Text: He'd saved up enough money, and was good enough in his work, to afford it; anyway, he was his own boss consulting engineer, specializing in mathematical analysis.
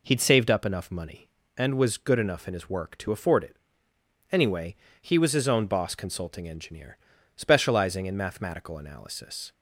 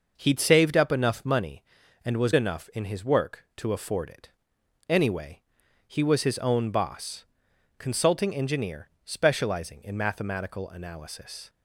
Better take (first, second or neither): first